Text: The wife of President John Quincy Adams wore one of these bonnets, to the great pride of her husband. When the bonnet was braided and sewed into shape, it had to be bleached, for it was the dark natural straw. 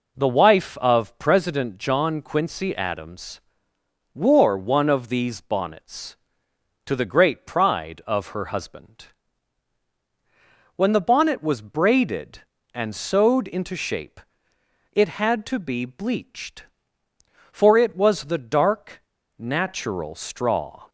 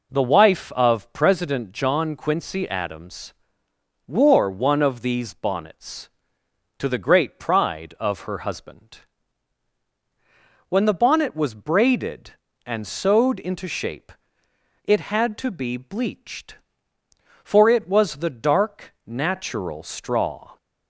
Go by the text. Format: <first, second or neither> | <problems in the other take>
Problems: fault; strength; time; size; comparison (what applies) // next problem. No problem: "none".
second | pauses between "Adams" and "wore"; noticeable; at 3.4 s; 0.72 s long; noticeable in the second // pauses between "dark" and "natural"; slight; at 19.0 s; 0.35 s long